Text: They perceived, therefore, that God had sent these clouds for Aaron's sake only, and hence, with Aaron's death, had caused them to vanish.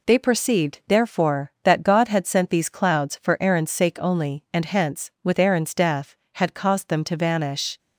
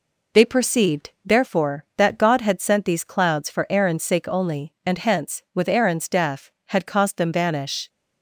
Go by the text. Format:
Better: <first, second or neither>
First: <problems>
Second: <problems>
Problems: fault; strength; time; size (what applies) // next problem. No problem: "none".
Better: first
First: none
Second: skips "to"; at 7.3 s